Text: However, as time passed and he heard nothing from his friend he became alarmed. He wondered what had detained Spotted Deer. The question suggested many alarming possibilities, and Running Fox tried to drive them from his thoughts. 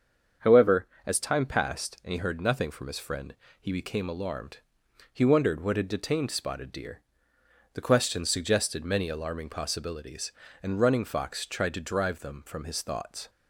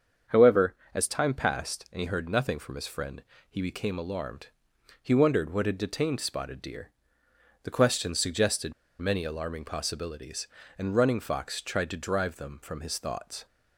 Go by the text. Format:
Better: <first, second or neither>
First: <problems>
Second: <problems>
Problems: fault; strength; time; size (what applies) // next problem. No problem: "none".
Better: first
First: starts louder than the rest; until 1.5 s; 7 dB // pauses between "friend" and "he"; slight; at 3.3 s; 0.25 s long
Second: starts louder than the rest; until 1.4 s; 7 dB // pauses between "friend" and "he"; slight; at 3.2 s; 0.26 s long // pauses between "suggested" and "many"; slight; at 8.7 s; 0.26 s long